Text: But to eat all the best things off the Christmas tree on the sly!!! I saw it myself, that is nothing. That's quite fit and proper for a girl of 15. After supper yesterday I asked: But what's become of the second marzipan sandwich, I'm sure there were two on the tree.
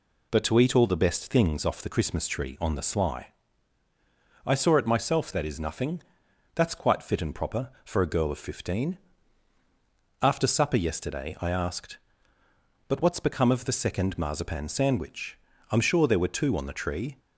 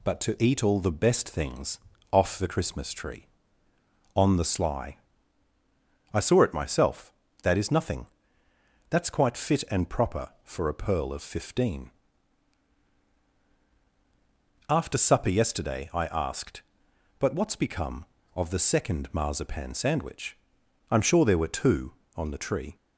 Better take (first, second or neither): first